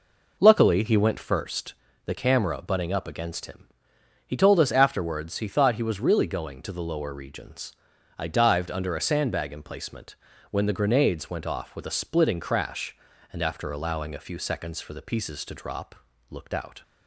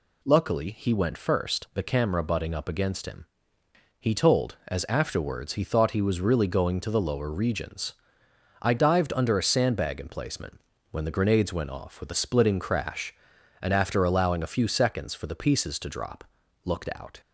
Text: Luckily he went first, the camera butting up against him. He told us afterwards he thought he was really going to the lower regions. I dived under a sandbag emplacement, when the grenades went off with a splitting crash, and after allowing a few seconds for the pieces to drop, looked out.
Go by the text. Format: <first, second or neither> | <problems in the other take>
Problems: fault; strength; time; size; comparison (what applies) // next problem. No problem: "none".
first | says "as" for "us"; at 4.6 s